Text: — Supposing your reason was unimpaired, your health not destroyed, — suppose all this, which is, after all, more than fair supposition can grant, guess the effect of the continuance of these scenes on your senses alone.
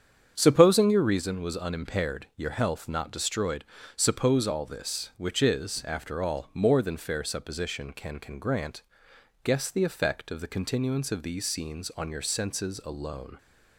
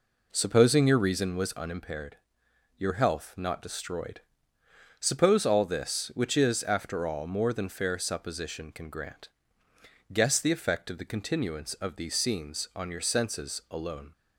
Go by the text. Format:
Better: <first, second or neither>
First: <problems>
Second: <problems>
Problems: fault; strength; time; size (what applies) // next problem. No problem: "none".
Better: second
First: starts louder than the rest; strong; until 1.3 s; 8 dB // says "can" twice; at 8.1 s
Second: none